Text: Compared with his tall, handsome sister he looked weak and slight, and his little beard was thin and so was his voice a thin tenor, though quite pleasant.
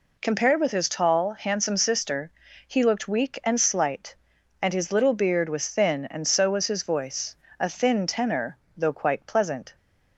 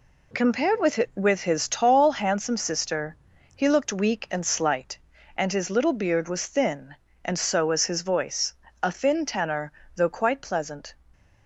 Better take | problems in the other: first | says "with" twice; at 1.1 s // pauses between "sister" and "he"; slight; at 3.1 s; 0.36 s long; slight in the first // pauses between "voice" and "a"; slight; at 8.5 s; 0.28 s long; slight in the first

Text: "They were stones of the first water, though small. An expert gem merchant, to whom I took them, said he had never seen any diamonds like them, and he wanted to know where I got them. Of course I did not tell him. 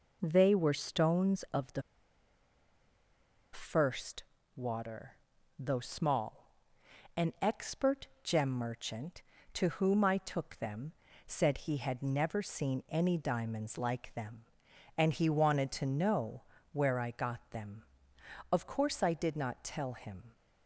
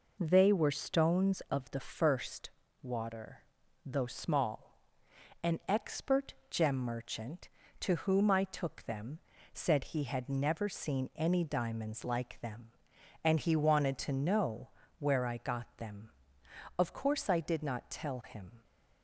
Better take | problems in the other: second | pauses between "the" and "first"; strong; at 1.8 s; 1.7 s long // pauses between "first" and "water"; slight; at 4.2 s; 0.32 s long; slight in the second // pauses between "expert" and "gem"; slight; at 8.0 s; 0.16 s long; slight in the second // pauses between "know" and "where"; slight; at 16.4 s; 0.28 s long; slight in the second

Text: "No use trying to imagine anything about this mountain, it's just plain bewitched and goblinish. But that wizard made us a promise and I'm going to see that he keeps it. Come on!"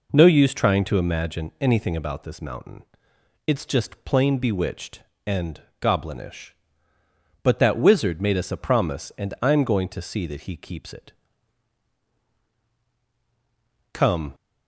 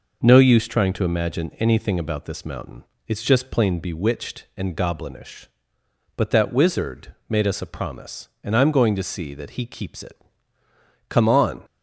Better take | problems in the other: second | pauses between "and" and "goblinish"; slight; at 5.6 s; 0.20 s long // stops before "on"; at 14.3 s

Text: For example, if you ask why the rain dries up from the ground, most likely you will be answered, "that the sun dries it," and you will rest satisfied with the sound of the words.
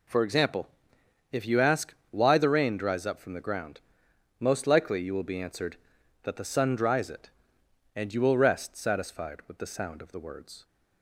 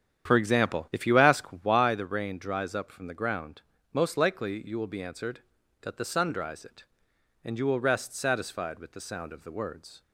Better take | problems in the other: first | starts louder than the rest; strong; until 1.9 s; 9 dB // pauses between "ask" and "why"; slight; at 1.4 s; 0.16 s long; slight in the first

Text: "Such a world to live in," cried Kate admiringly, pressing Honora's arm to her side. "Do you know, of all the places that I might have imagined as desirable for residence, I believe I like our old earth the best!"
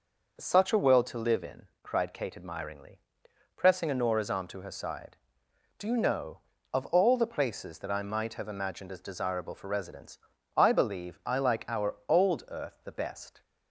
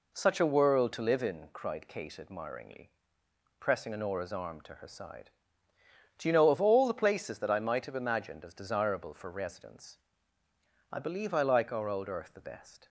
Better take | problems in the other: neither | none

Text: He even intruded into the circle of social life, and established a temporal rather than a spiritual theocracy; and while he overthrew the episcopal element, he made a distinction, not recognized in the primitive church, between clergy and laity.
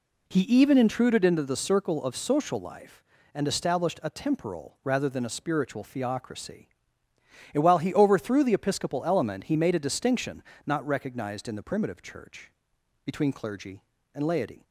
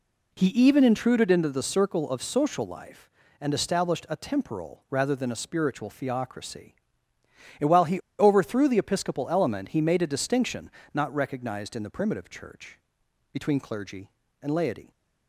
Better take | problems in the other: first | pauses between "he" and "overthrew"; slight; at 8.0 s; 0.18 s long

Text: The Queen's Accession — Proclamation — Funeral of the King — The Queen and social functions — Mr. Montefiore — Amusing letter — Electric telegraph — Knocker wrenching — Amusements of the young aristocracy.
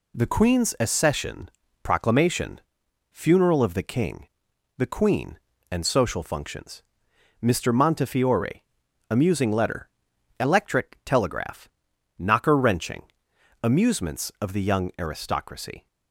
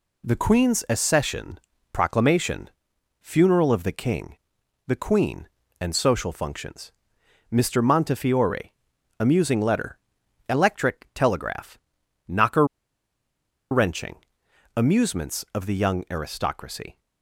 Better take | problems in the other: first | pauses between "Knocker" and "wrenching"; at 12.6 s; 1.0 s long

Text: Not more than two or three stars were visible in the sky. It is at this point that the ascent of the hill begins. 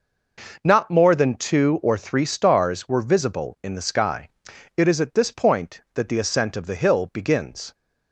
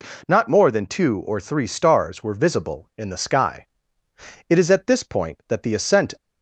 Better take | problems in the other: first | stops before "of the hill begins"; at 6.1 s

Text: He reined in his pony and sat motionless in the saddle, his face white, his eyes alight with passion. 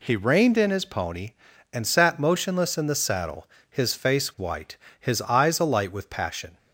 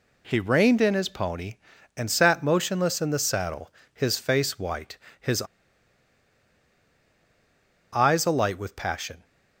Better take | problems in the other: first | pauses between "his" and "eyes"; strong; at 5.4 s; 2.5 s long

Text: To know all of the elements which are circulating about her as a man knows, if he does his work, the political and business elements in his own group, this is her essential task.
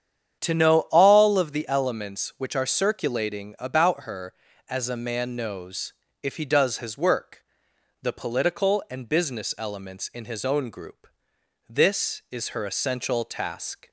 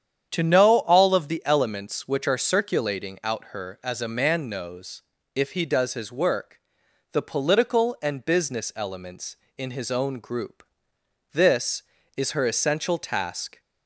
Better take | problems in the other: first | starts louder than the rest; strong; until 1.3 s; 8.5 dB; strong in the first // says "out" for "about"; at 3.2 s

